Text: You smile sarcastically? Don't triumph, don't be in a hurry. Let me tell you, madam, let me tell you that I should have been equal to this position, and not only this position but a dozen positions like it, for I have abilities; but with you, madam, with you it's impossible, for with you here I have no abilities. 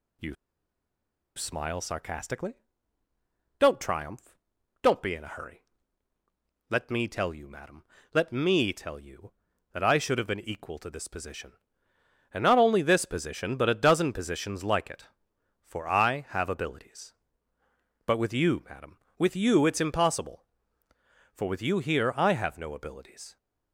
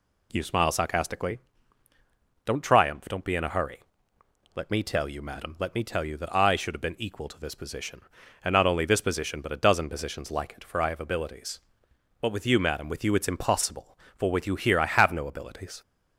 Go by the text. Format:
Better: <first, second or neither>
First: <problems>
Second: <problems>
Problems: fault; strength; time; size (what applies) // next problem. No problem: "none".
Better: second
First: pauses between "You" and "smile"; at 0.3 s; 1.0 s long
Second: none